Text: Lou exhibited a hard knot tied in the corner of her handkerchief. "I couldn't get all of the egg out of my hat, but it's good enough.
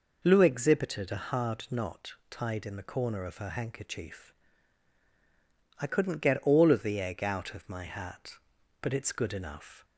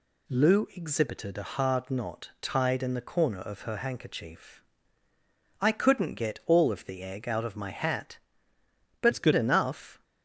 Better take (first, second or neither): first